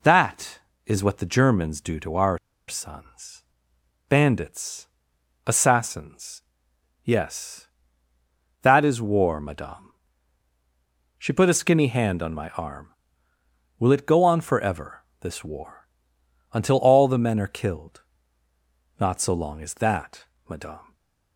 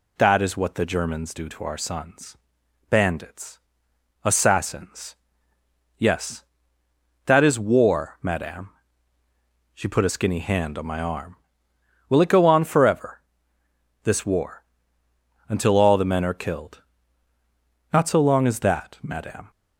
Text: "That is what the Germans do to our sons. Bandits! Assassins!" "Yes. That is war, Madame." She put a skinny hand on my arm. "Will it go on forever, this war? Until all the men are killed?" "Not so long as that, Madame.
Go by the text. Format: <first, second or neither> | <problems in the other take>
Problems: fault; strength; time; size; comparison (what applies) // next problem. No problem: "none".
second | pauses between "our" and "sons"; slight; at 2.3 s; 0.29 s long // stays silent after the last word; slight; from 20.8 s on; 0.5 s long